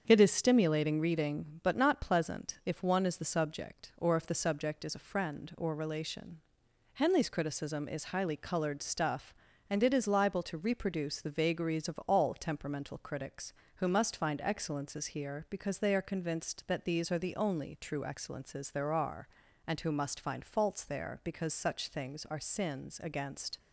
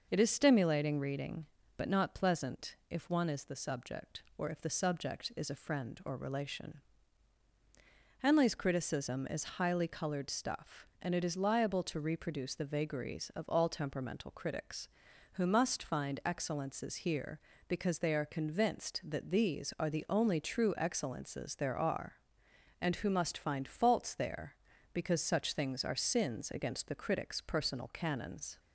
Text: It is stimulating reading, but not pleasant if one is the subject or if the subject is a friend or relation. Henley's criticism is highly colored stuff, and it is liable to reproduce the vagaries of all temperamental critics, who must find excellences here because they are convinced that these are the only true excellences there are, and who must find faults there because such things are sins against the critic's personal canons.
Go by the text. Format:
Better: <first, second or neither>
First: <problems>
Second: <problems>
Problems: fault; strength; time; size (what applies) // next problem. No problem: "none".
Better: second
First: starts louder than the rest; strong; until 1.0 s; 7.5 dB // stops before "the critic's personal canons"; at 23.5 s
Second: none